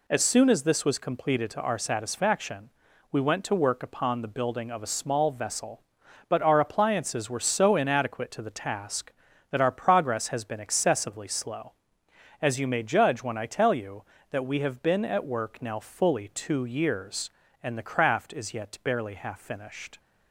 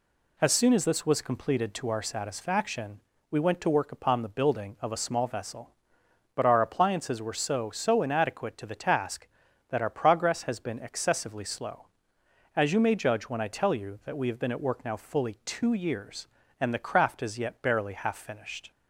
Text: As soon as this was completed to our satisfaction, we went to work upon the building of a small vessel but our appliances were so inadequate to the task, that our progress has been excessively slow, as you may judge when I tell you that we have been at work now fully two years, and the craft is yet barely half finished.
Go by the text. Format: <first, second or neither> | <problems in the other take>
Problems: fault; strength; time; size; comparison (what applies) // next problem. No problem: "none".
first | says "so" twice; at 7.7 s